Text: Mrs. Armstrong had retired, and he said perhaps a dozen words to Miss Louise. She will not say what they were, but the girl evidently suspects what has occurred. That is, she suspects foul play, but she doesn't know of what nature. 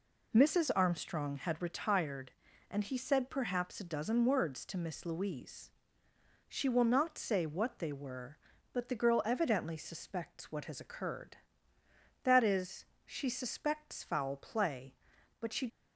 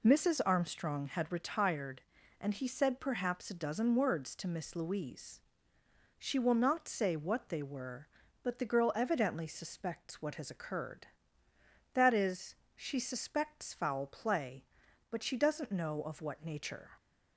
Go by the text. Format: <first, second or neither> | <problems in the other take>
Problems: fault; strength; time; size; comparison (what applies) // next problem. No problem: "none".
second | stops before "doesn't know of what nature"; at 15.6 s